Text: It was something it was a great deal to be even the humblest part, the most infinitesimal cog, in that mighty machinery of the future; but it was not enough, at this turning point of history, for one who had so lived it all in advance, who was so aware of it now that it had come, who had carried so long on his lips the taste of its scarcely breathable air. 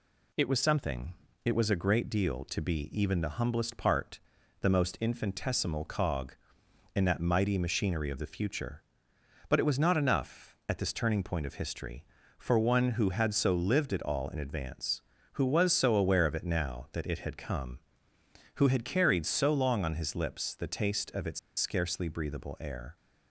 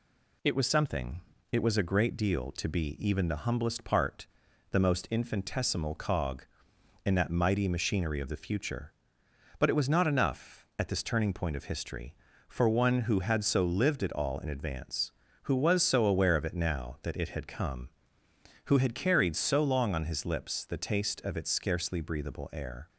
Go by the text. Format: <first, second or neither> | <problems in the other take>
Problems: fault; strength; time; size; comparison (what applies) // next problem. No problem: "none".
second | pauses between "something" and "it"; slight; at 1.1 s; 0.30 s long; slight in the second // pauses between "its" and "scarcely"; slight; at 21.3 s; 0.20 s long